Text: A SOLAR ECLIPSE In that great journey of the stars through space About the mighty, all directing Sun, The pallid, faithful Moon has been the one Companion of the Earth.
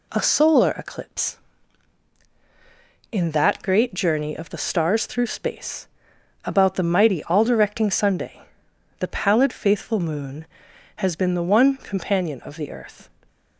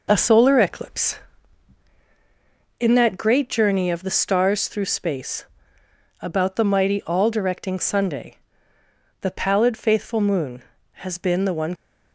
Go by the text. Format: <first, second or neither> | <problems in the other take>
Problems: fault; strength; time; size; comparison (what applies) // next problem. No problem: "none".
first | pauses between "space" and "About"; noticeable; at 5.4 s; 0.76 s long; noticeable in the first // stops before "Companion of the Earth"; at 11.7 s